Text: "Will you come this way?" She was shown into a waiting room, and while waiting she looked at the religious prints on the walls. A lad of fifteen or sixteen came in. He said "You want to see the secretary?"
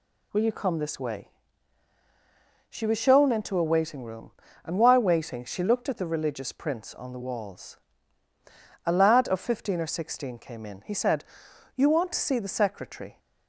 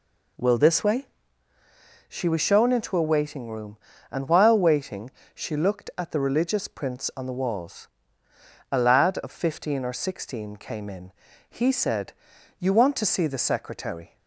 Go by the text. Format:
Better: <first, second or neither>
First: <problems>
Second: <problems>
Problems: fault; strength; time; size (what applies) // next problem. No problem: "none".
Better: first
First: pauses between "said" and "You"; noticeable; at 11.2 s; 0.50 s long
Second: skips "you come"; at 0.5 s // pauses between "waiting" and "she"; slight; at 5.0 s; 0.24 s long // pauses between "said" and "You"; noticeable; at 12.1 s; 0.46 s long